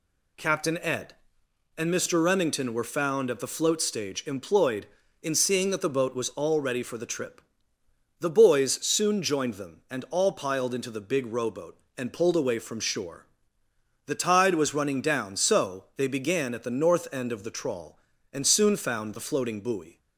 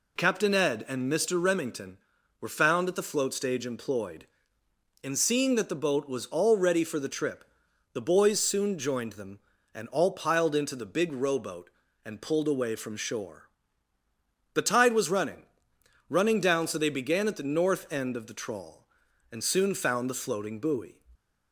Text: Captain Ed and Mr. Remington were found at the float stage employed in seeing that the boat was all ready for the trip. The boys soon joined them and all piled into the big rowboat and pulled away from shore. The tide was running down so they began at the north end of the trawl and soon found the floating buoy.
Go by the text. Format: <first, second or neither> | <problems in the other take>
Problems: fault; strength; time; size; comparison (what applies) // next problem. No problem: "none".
first | says "running" twice; at 16.0 s